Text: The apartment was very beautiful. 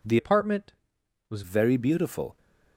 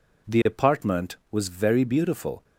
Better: second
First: changes voice from "apartment" to "was"; from 0.1 to 1.4 s; 1.3 s long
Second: none

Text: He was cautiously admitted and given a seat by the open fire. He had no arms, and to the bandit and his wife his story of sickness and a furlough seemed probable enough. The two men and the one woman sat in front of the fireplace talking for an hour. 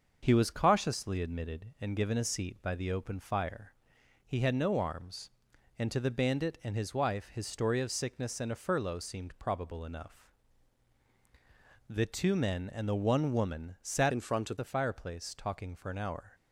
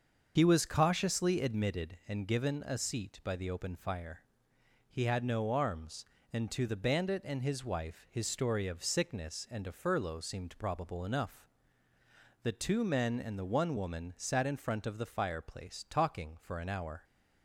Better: second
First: starts louder than the rest; until 1.2 s; 6.5 dB // changes voice from "in" to "of"; from 14.1 to 14.5 s; 0.4 s long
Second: starts louder than the rest; until 1.3 s; 6.5 dB

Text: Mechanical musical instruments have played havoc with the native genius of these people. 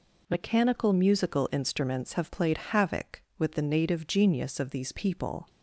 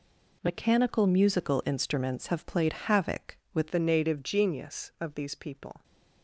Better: first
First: none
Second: changes voice at "the"; from 3.7 s on; 2.1 s long

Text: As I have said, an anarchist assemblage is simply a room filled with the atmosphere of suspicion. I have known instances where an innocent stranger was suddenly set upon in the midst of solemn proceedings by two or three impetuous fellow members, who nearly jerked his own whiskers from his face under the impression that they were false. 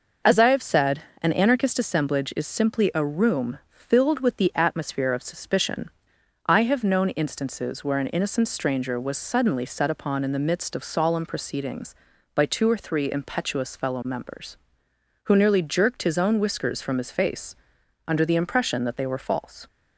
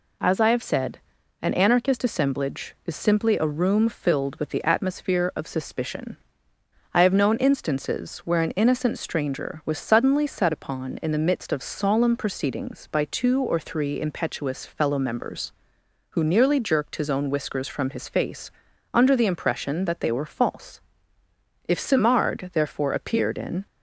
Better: first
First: pauses between "face" and "under"; noticeable; at 17.5 s; 0.52 s long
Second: pauses between "face" and "under"; at 18.4 s; 0.44 s long // goes on to say "If Simard therefore appeared in"; strong; from 21.6 s on; 1.9 s long

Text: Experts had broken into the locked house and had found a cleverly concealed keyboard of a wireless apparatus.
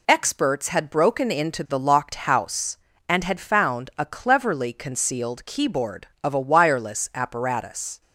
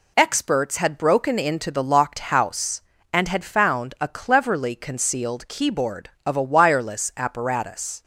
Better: neither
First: none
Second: none

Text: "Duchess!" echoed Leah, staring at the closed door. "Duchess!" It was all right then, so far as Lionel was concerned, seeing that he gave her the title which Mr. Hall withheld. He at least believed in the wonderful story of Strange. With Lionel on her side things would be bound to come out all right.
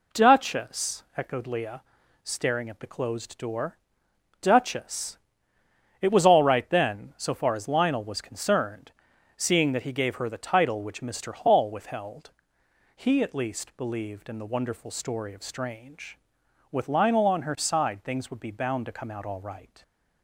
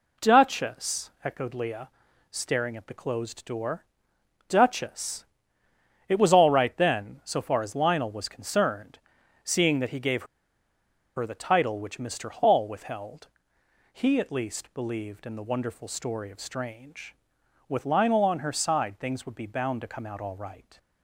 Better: first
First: none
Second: pauses between "gave" and "her"; noticeable; at 10.2 s; 0.92 s long

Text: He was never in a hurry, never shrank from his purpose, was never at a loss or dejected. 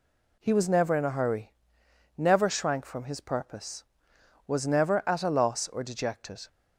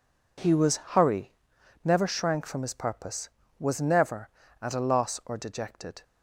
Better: first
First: none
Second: skips "never in a"; at 0.7 s

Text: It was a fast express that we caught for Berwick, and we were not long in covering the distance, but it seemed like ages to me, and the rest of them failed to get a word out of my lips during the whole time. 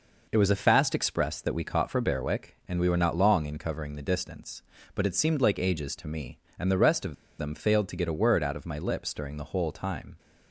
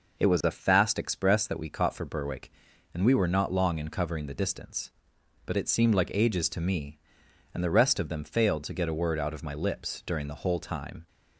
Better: second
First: pauses between "of" and "them"; slight; at 7.1 s; 0.25 s long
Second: none

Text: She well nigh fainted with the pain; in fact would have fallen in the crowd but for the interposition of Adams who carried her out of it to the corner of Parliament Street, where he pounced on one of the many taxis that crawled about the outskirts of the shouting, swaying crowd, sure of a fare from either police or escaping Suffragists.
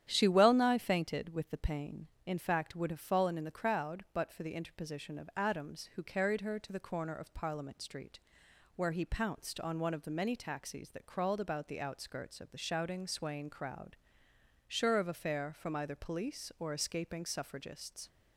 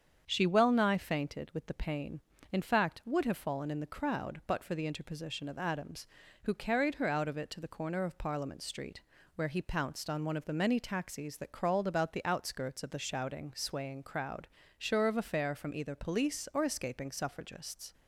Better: second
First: starts louder than the rest; strong; until 1.1 s; 10.5 dB // skips "out of it"; at 6.5 s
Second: starts louder than the rest; strong; until 1.2 s; 7.5 dB

